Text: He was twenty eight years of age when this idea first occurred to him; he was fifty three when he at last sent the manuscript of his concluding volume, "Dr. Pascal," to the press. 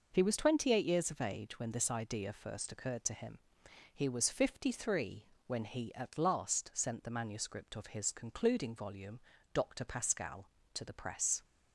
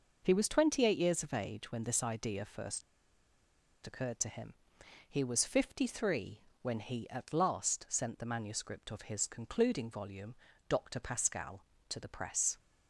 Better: first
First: pauses between "three" and "when"; slight; at 5.2 s; 0.18 s long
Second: pauses between "first" and "occurred"; at 2.8 s; 1.0 s long // pauses between "three" and "when"; slight; at 6.4 s; 0.18 s long

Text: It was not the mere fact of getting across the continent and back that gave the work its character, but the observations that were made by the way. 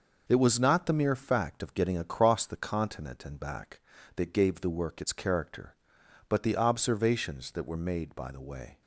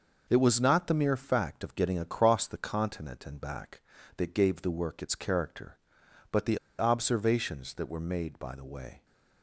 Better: first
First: none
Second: pauses between "the" and "observations"; slight; at 6.5 s; 0.20 s long

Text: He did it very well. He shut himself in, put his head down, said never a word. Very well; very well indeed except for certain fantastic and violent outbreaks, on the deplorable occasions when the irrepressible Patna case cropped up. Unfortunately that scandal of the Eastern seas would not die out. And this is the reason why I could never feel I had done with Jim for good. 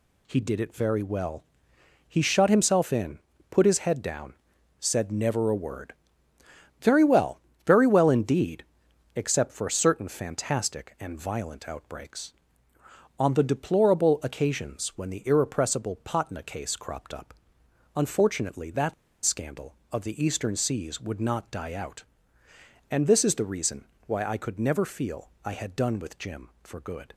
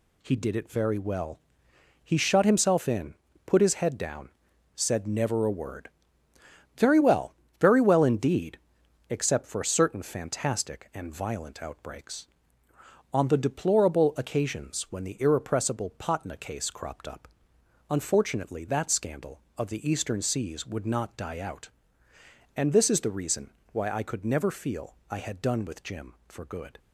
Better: second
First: pauses between "indeed" and "except"; noticeable; at 8.6 s; 0.54 s long // pauses between "that" and "scandal"; slight; at 18.9 s; 0.31 s long // pauses between "reason" and "why"; slight; at 23.8 s; 0.22 s long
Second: pauses between "indeed" and "except"; noticeable; at 8.5 s; 0.54 s long // pauses between "reason" and "why"; slight; at 23.4 s; 0.22 s long

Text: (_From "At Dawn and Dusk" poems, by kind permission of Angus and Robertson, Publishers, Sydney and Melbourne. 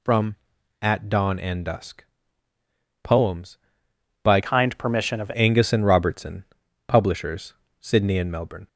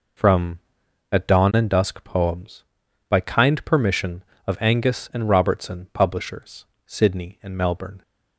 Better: second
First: pauses between "Dusk" and "poems"; at 2.0 s; 1.0 s long // changes voice from "kind" to "of"; from 4.4 to 5.3 s; 0.9 s long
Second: none

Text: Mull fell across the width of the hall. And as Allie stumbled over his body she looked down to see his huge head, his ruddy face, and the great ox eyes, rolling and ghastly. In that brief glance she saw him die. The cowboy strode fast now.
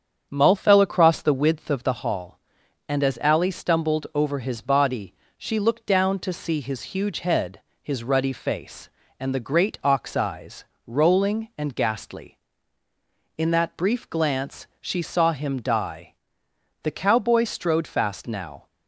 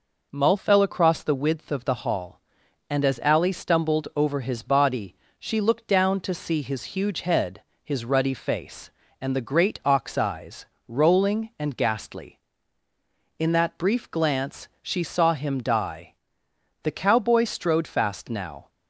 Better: second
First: starts louder than the rest; strong; until 1.9 s; 7.5 dB // pauses between "body" and "she"; slight; at 5.1 s; 0.26 s long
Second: pauses between "body" and "she"; slight; at 5.1 s; 0.26 s long

